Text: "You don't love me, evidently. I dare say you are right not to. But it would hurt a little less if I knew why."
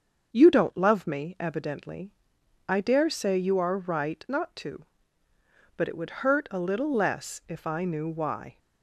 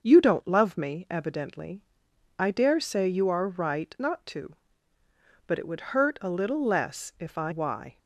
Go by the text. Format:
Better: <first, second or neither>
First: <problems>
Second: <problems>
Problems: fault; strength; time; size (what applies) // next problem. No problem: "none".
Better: first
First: starts louder than the rest; until 1.3 s; 6.5 dB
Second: starts louder than the rest; until 1.0 s; 6.5 dB // skips "knew"; at 7.5 s